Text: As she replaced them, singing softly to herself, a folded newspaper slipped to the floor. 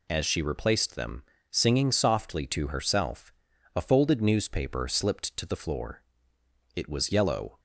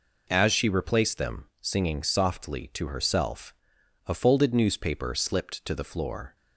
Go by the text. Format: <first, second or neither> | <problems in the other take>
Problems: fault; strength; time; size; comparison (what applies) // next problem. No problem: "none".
second | goes on to say "It was yellow"; noticeable; from 6.7 s on; 0.84 s long